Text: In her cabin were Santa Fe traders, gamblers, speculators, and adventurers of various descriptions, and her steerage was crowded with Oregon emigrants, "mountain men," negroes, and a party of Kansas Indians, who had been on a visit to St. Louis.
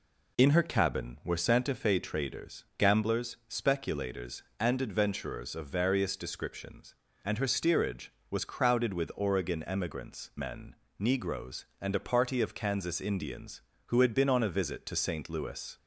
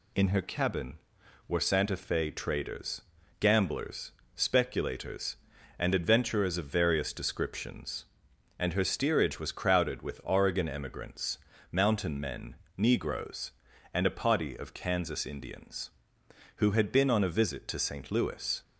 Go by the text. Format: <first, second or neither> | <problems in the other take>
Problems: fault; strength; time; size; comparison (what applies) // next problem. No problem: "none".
second | skips "mountain"; at 10.3 s